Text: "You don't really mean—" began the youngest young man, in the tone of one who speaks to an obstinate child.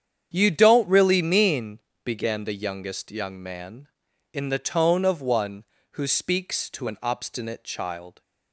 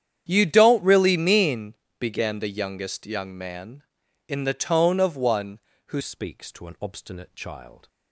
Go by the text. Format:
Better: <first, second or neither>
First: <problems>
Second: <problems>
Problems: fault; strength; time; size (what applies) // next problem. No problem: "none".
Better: first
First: starts louder than the rest; strong; until 1.3 s; 8.5 dB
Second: starts louder than the rest; strong; until 1.2 s; 9.5 dB // changes voice at "speaks"; from 6.0 s on; 1.8 s long